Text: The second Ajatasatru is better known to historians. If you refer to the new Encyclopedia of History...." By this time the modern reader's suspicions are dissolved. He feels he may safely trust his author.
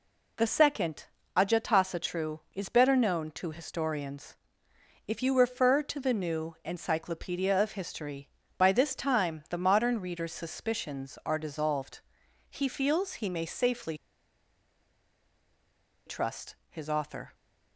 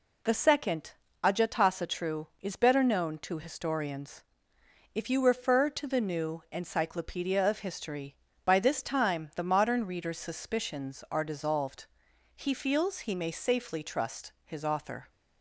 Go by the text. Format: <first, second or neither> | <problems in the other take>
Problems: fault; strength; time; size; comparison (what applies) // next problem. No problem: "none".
second | pauses between "second" and "Ajatasatru"; slight; at 1.0 s; 0.30 s long; slight in the second // pauses between "safely" and "trust"; strong; at 13.9 s; 2.1 s long